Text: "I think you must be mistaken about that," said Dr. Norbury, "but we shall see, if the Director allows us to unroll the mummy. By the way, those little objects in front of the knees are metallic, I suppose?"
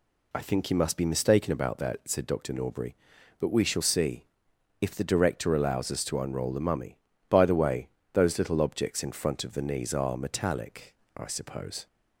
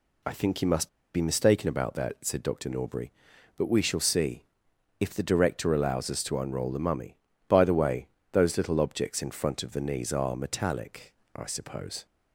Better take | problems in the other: first | pauses between "must" and "be"; slight; at 0.8 s; 0.27 s long

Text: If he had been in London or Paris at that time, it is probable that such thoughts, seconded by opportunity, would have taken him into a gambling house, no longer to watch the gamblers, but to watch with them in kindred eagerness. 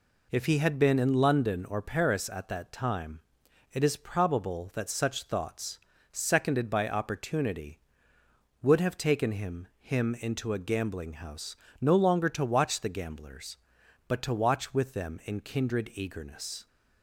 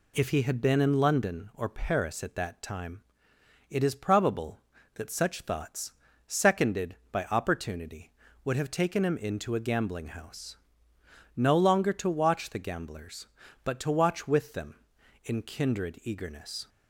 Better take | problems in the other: second | says "him" twice; at 9.8 s

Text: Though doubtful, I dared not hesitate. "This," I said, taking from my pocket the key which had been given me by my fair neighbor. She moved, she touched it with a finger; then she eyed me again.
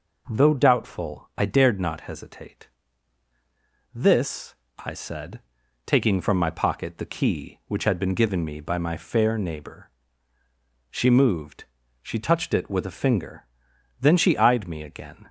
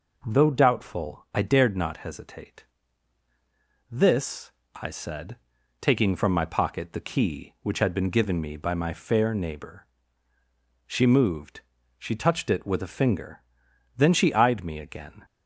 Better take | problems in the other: neither | none

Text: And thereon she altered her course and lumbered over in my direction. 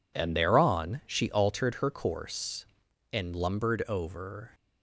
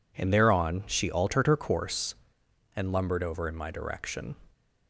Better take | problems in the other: second | stops before "in my direction"; at 4.5 s

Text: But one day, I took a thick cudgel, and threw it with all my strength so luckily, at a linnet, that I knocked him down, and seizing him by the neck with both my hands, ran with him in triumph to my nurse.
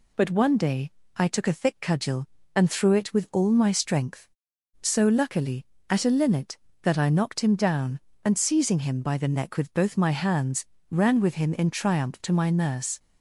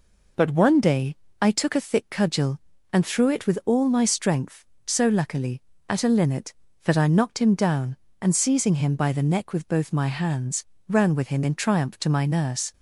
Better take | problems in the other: neither | none

